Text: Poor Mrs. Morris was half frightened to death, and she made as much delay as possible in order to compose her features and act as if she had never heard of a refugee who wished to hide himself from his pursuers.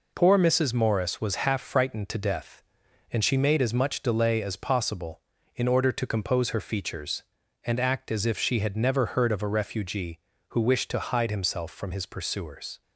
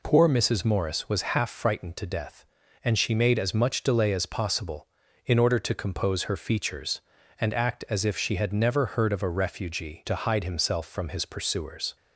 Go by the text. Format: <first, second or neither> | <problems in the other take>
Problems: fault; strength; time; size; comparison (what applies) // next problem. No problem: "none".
first | skips "who wished"; at 10.0 s